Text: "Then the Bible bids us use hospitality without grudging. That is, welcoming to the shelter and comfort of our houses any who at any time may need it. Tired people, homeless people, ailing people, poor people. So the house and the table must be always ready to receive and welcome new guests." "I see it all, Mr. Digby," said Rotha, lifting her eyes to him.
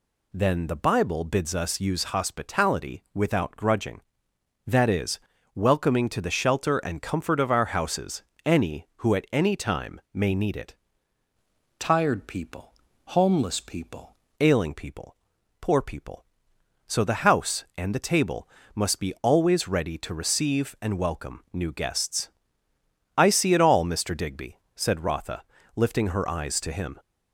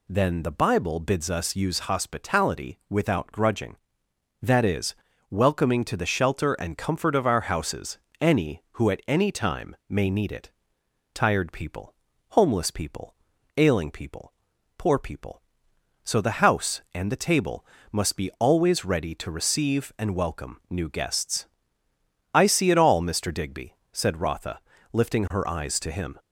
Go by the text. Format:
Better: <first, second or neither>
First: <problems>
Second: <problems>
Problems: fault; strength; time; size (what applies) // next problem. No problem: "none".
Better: second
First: pauses between "houses" and "any"; slight; at 8.2 s; 0.24 s long // changes voice from "Tired" to "people"; from 11.7 to 14.1 s; 2.4 s long // pauses between "table" and "must"; slight; at 18.4 s; 0.26 s long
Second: pauses between "houses" and "any"; slight; at 7.9 s; 0.24 s long // pauses between "table" and "must"; slight; at 17.6 s; 0.26 s long